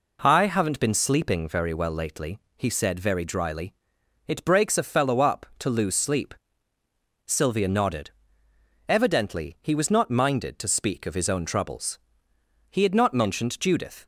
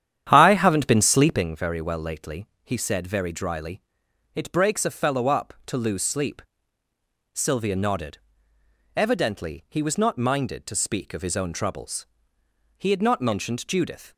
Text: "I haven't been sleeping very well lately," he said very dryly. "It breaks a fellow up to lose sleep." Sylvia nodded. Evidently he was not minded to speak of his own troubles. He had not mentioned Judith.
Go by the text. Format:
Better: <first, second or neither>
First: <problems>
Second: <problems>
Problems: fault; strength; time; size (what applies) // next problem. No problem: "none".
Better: first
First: none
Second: starts louder than the rest; strong; until 1.5 s; 10 dB